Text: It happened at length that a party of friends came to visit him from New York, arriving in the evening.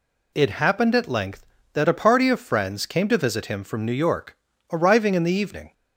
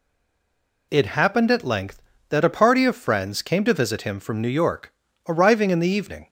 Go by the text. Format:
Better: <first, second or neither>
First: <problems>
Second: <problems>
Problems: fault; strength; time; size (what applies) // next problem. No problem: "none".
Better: first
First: none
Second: stays silent before the first word; slight; until 0.9 s; 0.9 s long